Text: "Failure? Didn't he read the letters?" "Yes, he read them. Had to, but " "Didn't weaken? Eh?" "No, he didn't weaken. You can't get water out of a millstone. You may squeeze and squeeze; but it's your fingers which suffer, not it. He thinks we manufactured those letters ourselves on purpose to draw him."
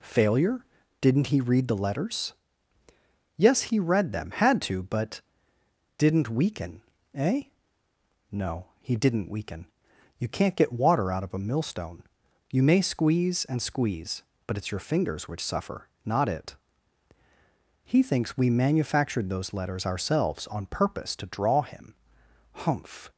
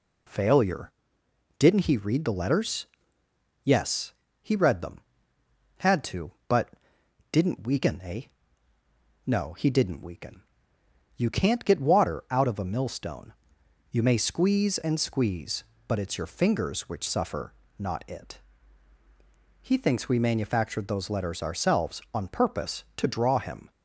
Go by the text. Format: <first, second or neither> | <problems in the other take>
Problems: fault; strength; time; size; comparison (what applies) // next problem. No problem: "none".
second | goes on to say "Humph"; from 22.5 s on; 0.58 s long